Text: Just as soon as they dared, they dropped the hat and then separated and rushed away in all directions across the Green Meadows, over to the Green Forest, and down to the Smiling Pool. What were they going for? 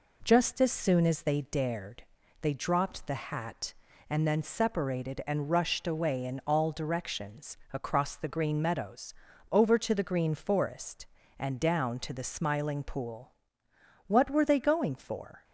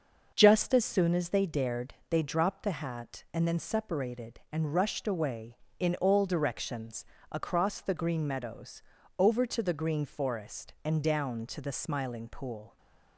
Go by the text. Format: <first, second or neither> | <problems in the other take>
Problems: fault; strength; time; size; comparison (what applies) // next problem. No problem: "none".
first | starts louder than the rest; until 1.3 s; 6 dB // pauses between "directions" and "across"; slight; at 7.0 s; 0.26 s long; slight in the first // stops before "What were they going for"; at 12.7 s